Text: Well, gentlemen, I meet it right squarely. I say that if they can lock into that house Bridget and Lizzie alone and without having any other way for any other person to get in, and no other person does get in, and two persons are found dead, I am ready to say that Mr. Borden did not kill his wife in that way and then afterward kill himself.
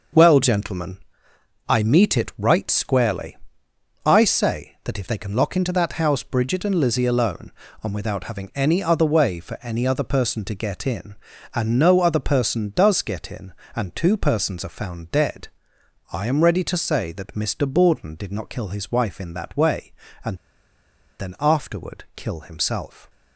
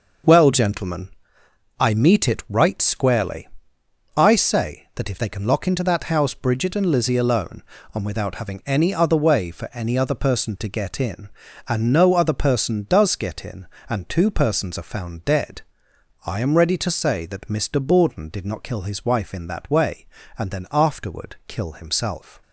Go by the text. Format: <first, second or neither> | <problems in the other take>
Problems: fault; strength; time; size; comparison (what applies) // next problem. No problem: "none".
second | starts louder than the rest; noticeable; until 1.8 s; 6 dB; noticeable in the second // pauses between "and" and "then"; noticeable; at 20.3 s; 0.82 s long